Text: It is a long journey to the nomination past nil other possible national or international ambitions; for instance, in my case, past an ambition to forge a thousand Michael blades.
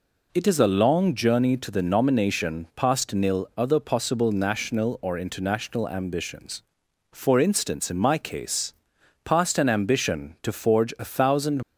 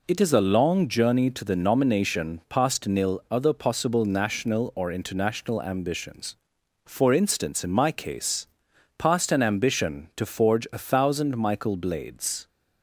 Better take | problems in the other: second | stops before "Michael blades"; at 11.6 s

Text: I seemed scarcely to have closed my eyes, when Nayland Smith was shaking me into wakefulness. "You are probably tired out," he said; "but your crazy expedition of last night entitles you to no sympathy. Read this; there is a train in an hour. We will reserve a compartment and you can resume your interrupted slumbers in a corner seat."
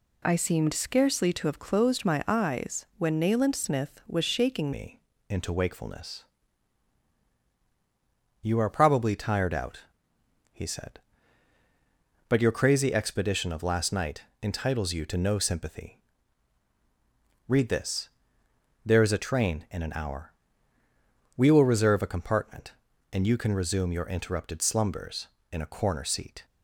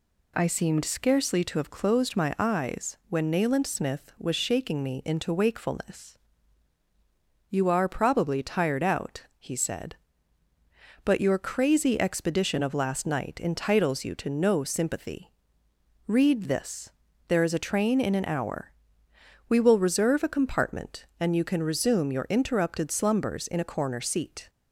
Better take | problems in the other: second | changes voice at "me"; from 4.7 s on; 21.7 s long // pauses between "me" and "into"; slight; at 5.0 s; 0.28 s long // pauses between "night" and "entitles"; slight; at 14.2 s; 0.20 s long

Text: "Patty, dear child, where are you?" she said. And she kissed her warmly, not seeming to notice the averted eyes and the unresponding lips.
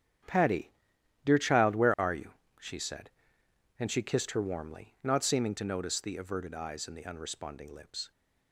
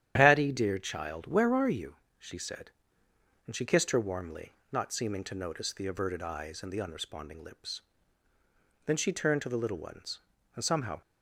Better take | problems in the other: first | starts louder than the rest; strong; until 1.1 s; 10.5 dB; strong in the first // goes on to say "Then she turned to the little ones and somehow"; strong; from 8.8 s on; 2.1 s long

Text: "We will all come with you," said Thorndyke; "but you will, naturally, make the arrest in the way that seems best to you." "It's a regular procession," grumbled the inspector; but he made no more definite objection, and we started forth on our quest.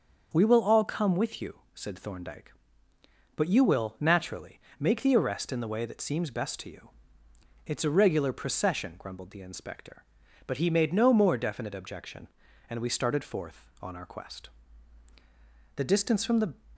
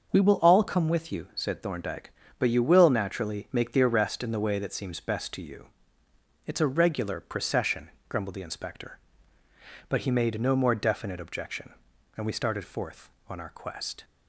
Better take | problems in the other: second | starts louder than the rest; until 1.3 s; 6.5 dB; also in the second // goes on to say "The distance from the"; noticeable; from 15.7 s on; 0.78 s long

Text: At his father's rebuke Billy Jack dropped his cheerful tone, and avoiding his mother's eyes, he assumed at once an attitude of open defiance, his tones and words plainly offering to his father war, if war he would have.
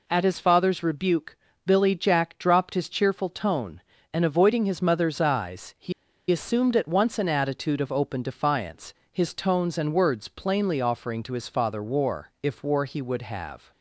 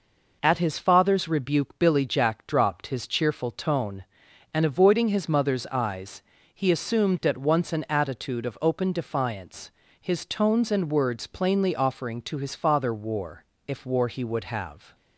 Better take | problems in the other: second | pauses between "rebuke" and "Billy"; slight; at 1.3 s; 0.30 s long // pauses between "he" and "assumed"; at 5.9 s; 0.38 s long

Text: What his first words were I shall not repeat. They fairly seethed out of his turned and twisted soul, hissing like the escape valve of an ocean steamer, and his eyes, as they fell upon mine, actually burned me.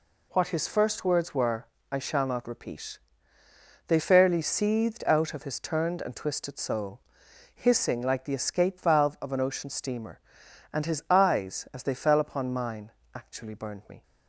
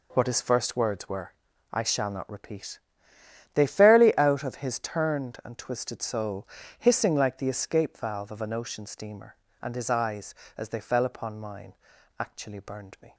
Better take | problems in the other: first | pauses between "were" and "I"; at 1.3 s; 0.40 s long; slight in the first // skips "seethed"; at 4.1 s

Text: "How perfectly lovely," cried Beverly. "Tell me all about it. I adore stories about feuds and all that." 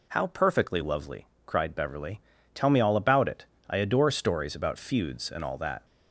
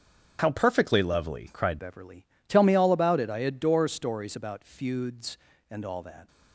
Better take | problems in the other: first | starts louder than the rest; strong; until 1.4 s; 7 dB // changes voice at "Beverly"; from 1.7 s on; 4.5 s long

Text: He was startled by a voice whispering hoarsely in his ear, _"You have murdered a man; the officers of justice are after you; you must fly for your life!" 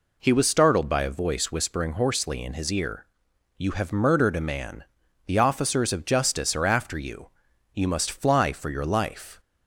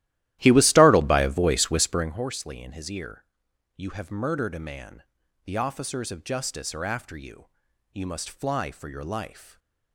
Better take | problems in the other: first | starts louder than the rest; strong; until 2.2 s; 14.5 dB // stays silent after the last word; slight; from 9.4 s on; 0.5 s long

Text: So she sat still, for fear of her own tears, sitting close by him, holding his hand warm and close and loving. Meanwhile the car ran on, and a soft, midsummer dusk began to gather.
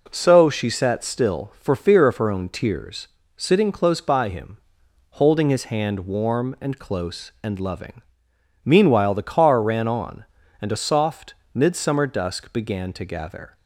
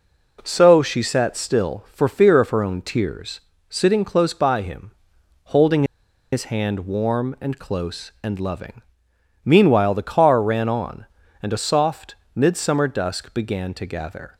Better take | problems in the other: first | pauses between "holding" and "his"; noticeable; at 5.8 s; 0.49 s long

